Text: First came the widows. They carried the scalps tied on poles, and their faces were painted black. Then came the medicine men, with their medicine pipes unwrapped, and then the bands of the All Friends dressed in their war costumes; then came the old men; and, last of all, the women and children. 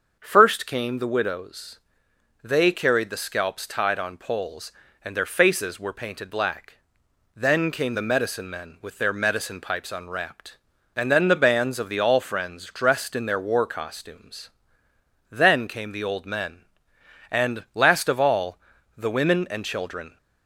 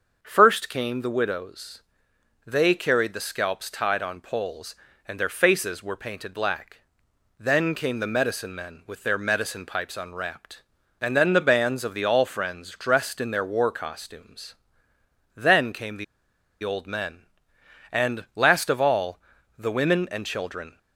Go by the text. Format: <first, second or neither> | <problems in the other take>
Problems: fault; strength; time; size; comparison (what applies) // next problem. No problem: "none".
first | starts louder than the rest; until 1.2 s; 6.5 dB; also in the first // pauses between "the" and "old"; noticeable; at 16.0 s; 0.58 s long